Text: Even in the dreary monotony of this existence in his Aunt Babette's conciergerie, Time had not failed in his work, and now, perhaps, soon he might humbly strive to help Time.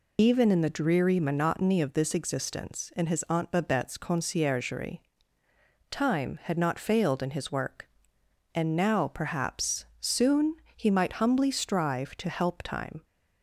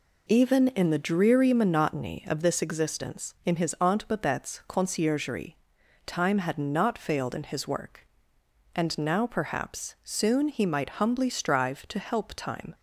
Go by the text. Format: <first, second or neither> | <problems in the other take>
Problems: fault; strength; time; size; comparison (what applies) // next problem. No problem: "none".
second | loses the start of "Even"; at 0.1 s; 45 ms // pauses between "soon" and "he"; slight; at 10.5 s; 0.22 s long